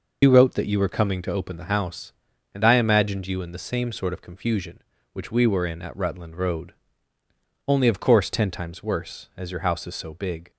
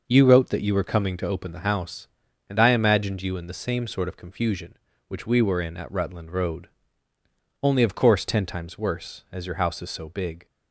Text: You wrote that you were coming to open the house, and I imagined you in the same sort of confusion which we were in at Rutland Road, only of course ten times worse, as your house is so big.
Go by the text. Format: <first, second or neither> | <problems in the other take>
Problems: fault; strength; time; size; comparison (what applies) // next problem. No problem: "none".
second | loses the start of "You"; at 0.2 s; 100 ms